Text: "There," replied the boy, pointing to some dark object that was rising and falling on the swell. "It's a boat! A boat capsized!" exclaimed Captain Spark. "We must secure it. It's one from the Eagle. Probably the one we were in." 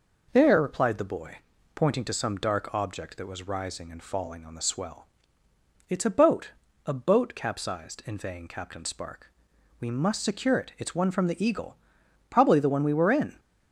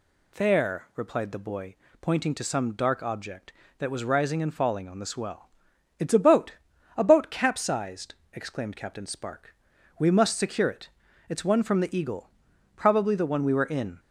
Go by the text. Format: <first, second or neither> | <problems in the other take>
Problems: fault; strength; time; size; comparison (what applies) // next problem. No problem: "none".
second | says "inveighing" for "exclaimed"; at 8.0 s